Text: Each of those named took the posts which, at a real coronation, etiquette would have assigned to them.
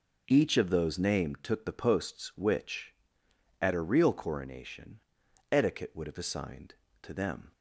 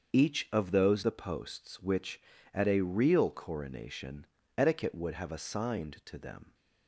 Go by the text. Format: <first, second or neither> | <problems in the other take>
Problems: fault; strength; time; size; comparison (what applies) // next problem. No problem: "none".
first | starts louder than the rest; until 1.1 s; 6.5 dB // skips "named took"; at 1.0 s